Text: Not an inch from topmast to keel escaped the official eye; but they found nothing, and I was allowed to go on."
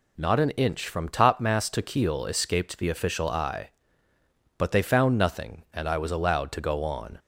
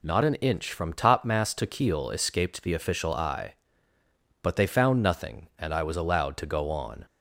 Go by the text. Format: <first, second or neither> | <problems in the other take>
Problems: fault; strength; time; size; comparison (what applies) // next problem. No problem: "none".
neither | none